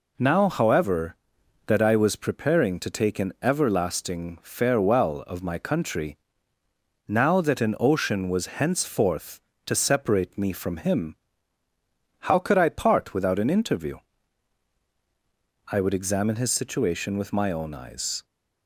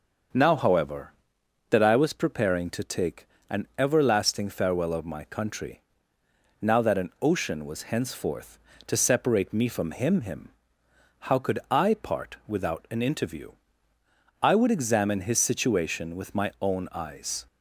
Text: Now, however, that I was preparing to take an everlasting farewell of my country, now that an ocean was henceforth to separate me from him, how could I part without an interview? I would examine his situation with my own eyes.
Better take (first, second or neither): first